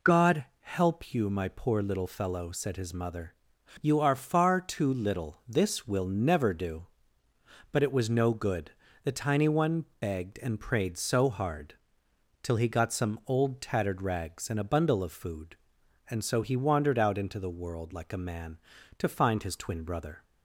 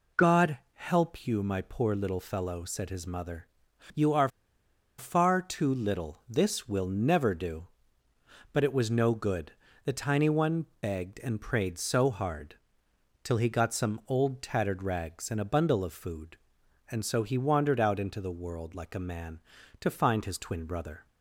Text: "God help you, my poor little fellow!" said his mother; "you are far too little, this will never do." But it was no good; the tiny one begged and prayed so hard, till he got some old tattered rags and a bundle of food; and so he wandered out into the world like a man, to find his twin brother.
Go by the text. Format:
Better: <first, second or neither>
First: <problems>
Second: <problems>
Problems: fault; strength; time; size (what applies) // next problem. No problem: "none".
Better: first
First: pauses between "God" and "help"; slight; at 0.4 s; 0.16 s long // pauses between "one" and "begged"; slight; at 9.8 s; 0.16 s long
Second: pauses between "God" and "help"; slight; at 0.5 s; 0.16 s long // pauses between "are" and "far"; noticeable; at 4.2 s; 0.70 s long // pauses between "one" and "begged"; slight; at 10.6 s; 0.16 s long